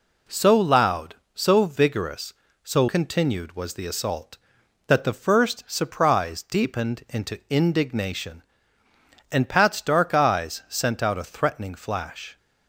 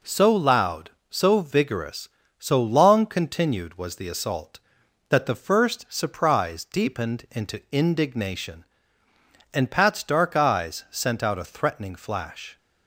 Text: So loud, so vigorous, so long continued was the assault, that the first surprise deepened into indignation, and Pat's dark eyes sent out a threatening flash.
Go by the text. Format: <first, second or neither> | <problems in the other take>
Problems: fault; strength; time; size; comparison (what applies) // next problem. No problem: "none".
second | skips "long"; at 2.8 s